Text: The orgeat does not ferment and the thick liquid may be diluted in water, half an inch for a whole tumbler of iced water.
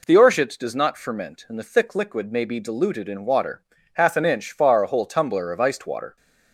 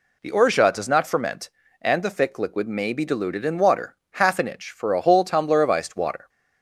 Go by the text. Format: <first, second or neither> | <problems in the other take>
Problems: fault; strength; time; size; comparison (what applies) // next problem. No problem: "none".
second | says "far" for "for"; at 4.5 s